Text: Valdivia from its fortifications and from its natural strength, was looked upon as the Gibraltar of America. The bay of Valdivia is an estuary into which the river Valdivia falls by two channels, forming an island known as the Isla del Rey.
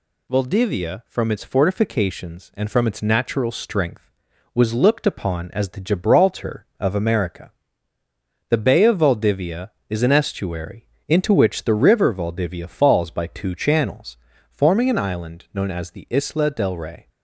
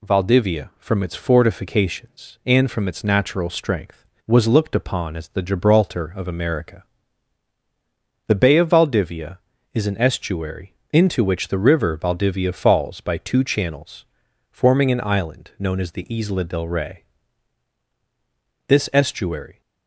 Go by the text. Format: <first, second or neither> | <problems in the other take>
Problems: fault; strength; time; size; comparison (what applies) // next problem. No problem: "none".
first | pauses between "estuary" and "into"; slight; at 10.7 s; 0.18 s long; slight in the first // goes on to say "This estuary"; noticeable; from 18.6 s on; 0.94 s long